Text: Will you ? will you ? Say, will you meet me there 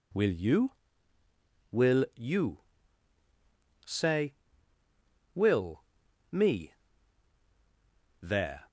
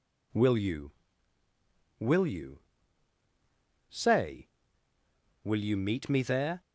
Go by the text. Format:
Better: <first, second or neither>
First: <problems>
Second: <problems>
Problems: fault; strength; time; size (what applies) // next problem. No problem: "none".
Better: second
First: skips "you meet"; at 6.0 s // pauses between "me" and "there"; strong; at 6.7 s; 1.4 s long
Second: none